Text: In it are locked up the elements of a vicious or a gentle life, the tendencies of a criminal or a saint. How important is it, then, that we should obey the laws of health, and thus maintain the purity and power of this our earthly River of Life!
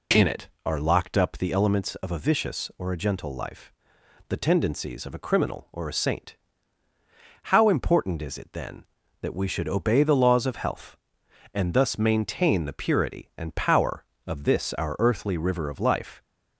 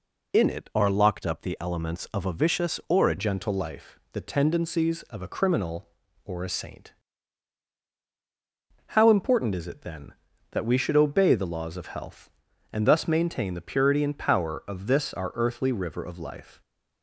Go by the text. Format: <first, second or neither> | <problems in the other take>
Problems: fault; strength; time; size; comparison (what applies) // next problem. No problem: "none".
first | changes voice at "gentle"; from 3.1 s on; 13.5 s long